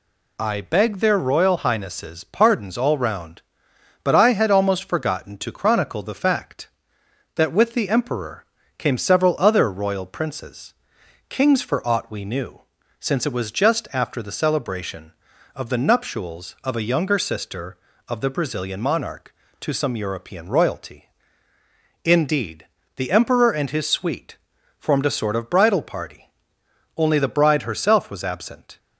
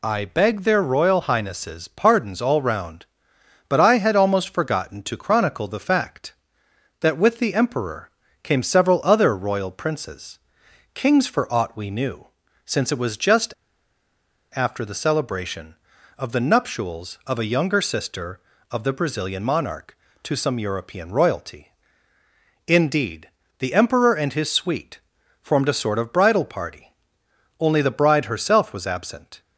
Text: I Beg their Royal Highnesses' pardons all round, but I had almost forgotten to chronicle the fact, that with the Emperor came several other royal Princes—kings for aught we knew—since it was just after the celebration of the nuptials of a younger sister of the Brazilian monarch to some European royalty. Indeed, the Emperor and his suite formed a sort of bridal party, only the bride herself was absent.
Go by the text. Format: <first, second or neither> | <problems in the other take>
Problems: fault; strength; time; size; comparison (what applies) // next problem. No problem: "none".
first | pauses between "Emperor" and "came"; slight; at 8.0 s; 0.32 s long; slight in the first // pauses between "just" and "after"; at 13.5 s; 1.0 s long // pauses between "suite" and "formed"; at 24.9 s; 0.44 s long; also in the first